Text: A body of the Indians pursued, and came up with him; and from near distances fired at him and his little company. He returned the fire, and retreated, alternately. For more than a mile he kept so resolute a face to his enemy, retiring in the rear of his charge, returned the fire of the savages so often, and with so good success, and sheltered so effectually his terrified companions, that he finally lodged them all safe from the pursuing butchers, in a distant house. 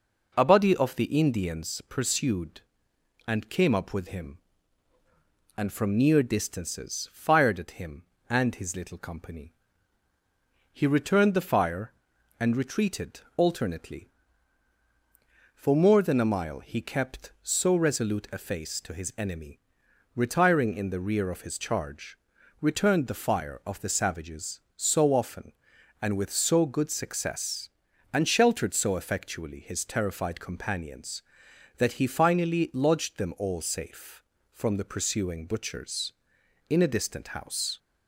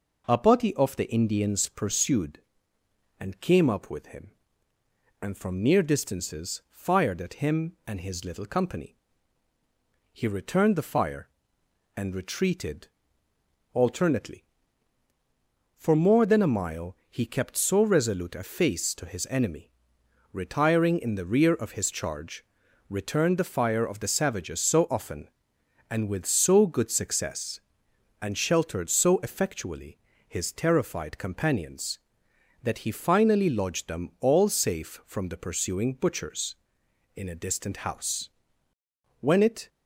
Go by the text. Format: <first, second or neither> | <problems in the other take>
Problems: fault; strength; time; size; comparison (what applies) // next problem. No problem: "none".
first | pauses between "effectually" and "his"; slight; at 29.9 s; 0.28 s long // goes on to say "When it"; slight; from 39.2 s on; 0.48 s long